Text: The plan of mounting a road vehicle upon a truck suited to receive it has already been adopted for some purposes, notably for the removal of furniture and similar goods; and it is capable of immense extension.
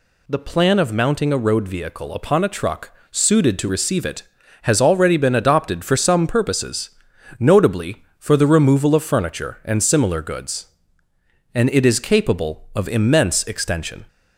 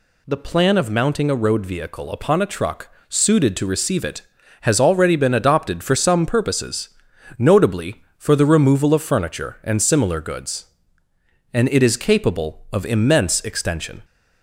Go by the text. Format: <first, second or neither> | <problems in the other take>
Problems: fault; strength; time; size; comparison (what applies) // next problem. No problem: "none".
neither | pauses between "truck" and "suited"; slight; the same in both